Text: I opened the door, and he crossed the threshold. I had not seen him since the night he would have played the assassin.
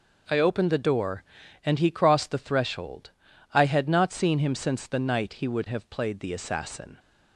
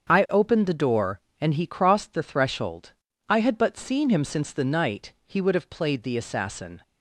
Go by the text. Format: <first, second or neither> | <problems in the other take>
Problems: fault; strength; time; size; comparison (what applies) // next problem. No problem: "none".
first | starts louder than the rest; strong; until 1.1 s; 7.5 dB // says "but" for "not"; at 3.5 s